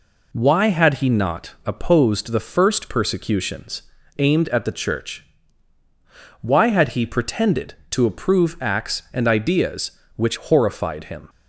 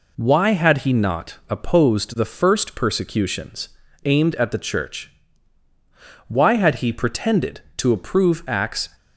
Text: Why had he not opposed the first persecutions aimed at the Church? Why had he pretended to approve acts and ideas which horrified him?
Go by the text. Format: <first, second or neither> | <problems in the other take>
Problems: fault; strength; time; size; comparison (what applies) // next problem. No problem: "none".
first | pauses between "persecutions" and "aimed"; slight; at 3.6 s; 0.36 s long; slight in the first // stops before "and ideas which horrified him"; at 8.9 s